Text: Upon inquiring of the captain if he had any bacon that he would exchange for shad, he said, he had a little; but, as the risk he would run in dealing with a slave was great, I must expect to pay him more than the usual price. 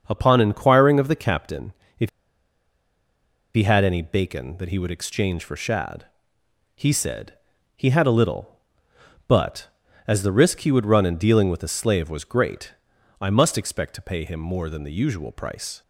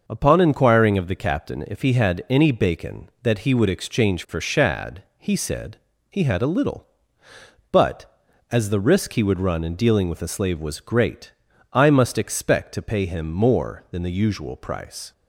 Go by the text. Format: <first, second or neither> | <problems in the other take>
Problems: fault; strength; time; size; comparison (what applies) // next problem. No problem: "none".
second | starts louder than the rest; until 1.0 s; 6.5 dB; noticeable in the second // pauses between "captain" and "if"; slight; at 1.7 s; 0.24 s long // pauses between "if" and "he"; strong; at 2.0 s; 1.4 s long